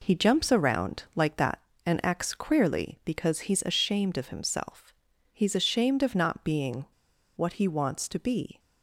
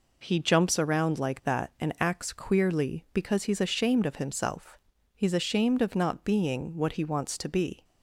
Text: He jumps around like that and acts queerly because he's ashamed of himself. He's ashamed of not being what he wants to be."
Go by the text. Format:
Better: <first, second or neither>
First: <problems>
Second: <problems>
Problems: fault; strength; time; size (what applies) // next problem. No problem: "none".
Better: second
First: pauses between "being" and "what"; noticeable; at 6.8 s; 0.49 s long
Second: none